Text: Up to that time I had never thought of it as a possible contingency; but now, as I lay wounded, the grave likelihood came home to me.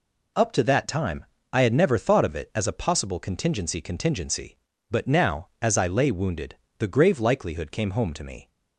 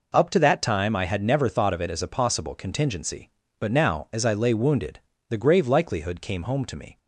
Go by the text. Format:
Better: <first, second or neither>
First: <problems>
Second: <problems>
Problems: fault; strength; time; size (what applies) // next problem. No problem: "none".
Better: second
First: pauses between "time" and "I"; slight; at 1.2 s; 0.26 s long // says "contingency" twice; at 3.8 s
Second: none